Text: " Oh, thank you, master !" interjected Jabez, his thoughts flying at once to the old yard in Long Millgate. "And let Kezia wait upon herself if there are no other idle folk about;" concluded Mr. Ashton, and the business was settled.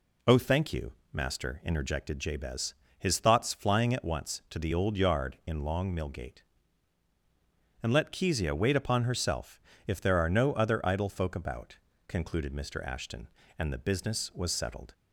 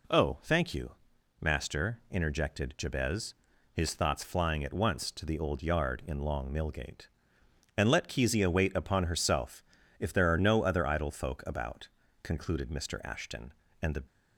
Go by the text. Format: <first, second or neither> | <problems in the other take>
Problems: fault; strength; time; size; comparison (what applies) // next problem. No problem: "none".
first | pauses between "herself" and "if"; slight; at 9.6 s; 0.36 s long; slight in the first // stops before "business was settled"; at 14.0 s